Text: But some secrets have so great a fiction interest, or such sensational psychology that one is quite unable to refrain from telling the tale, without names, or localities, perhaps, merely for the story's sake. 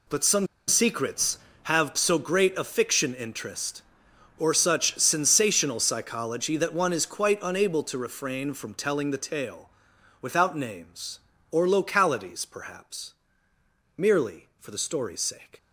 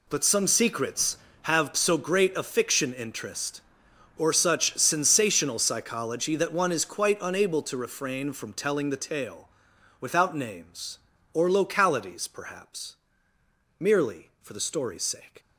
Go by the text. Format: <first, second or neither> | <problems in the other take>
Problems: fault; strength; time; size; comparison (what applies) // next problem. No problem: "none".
second | pauses between "some" and "secrets"; slight; at 0.4 s; 0.21 s long